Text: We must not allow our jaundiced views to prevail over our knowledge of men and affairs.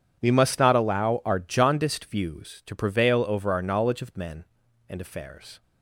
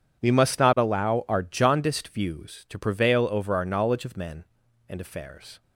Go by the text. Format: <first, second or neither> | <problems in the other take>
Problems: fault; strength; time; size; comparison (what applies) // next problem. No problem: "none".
neither | none